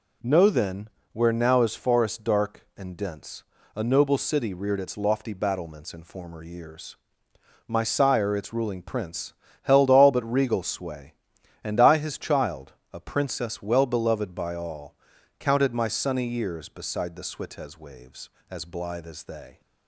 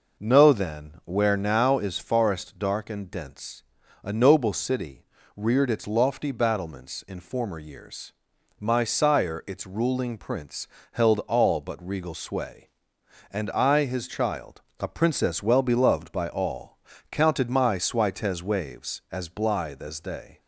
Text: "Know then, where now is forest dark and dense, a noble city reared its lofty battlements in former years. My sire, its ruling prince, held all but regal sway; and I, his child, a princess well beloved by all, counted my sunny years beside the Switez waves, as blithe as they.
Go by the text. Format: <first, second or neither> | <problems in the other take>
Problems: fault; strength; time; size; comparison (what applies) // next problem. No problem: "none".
first | pauses between "city" and "reared"; slight; at 5.0 s; 0.32 s long // skips "sunny years beside the"; at 17.7 s